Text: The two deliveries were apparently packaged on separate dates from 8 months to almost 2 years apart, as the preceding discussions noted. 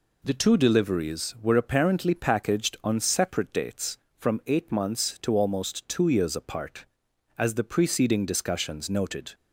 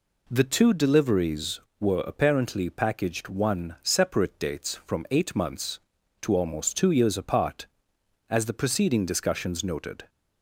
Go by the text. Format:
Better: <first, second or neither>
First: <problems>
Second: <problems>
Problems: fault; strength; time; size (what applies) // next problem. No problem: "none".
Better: first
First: none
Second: says "one" for "on"; at 3.2 s